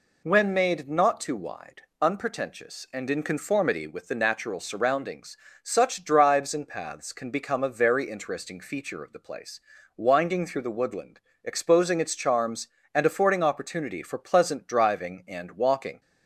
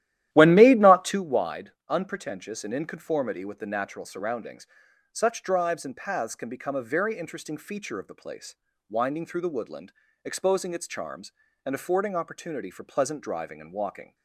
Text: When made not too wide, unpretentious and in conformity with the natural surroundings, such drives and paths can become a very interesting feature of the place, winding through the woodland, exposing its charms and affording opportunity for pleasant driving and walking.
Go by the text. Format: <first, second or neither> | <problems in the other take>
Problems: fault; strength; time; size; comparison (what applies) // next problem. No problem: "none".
first | starts louder than the rest; strong; until 1.2 s; 13 dB